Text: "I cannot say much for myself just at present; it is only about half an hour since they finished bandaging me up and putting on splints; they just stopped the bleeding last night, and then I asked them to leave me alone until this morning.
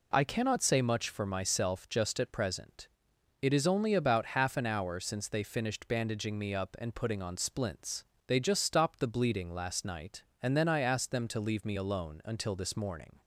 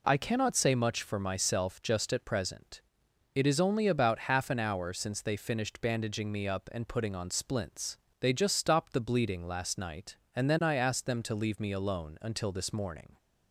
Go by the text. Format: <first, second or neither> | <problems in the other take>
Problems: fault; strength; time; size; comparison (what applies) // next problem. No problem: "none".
neither | none